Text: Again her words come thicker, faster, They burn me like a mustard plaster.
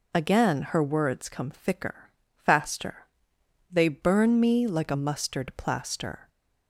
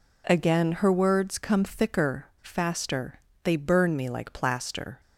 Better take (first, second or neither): first